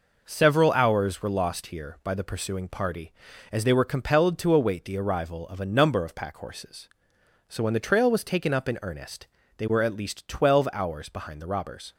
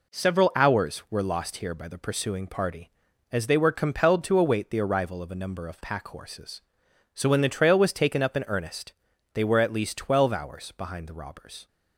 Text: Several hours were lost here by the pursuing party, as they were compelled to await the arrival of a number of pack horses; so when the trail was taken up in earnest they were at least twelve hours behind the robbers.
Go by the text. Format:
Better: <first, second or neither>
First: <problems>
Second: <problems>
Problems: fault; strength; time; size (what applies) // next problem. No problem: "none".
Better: neither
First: pauses between "earnest" and "they"; slight; at 9.2 s; 0.32 s long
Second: pauses between "earnest" and "they"; at 8.9 s; 0.40 s long